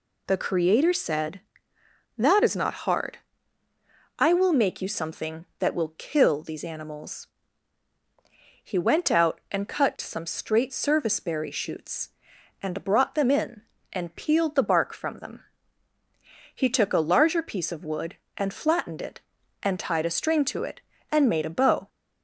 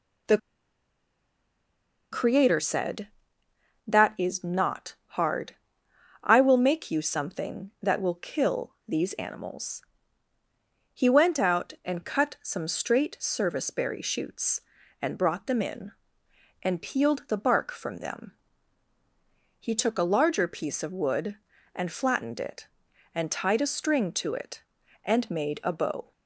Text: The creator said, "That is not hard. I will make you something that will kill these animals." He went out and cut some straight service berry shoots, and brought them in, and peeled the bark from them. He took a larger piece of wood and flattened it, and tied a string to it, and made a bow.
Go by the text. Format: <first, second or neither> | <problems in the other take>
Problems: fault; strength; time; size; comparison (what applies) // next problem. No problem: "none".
first | pauses between "The" and "creator"; strong; at 0.3 s; 1.7 s long // pauses between "not" and "hard"; slight; at 4.9 s; 0.20 s long